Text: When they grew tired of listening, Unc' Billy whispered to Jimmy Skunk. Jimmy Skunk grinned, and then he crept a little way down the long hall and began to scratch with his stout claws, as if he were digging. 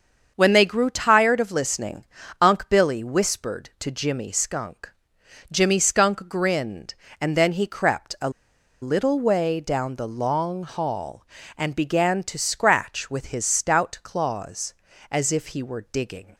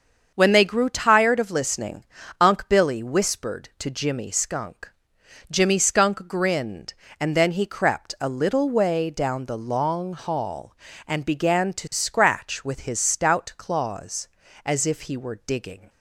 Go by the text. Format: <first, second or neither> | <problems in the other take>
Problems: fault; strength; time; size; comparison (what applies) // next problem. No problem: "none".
second | starts louder than the rest; until 1.3 s; 7 dB; also in the second // pauses between "a" and "little"; noticeable; at 8.2 s; 0.52 s long